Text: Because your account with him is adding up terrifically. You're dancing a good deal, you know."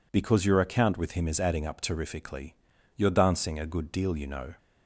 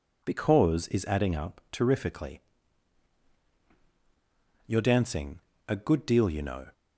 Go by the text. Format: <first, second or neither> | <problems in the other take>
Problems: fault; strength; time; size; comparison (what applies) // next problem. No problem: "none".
first | skips "your account with him"; at 0.8 s // pauses between "dancing" and "a"; slight; at 5.4 s; 0.26 s long